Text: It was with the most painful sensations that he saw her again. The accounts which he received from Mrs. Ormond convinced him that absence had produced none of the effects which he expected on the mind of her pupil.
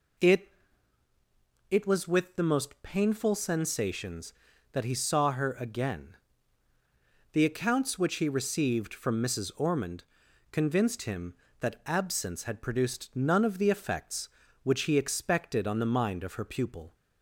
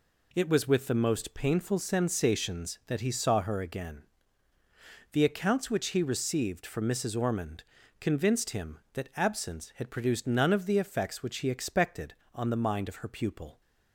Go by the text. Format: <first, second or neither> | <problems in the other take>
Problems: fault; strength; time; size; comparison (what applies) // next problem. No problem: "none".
second | says "It" twice; at 1.6 s // pauses between "Ormond" and "convinced"; noticeable; at 10.0 s; 0.46 s long; slight in the second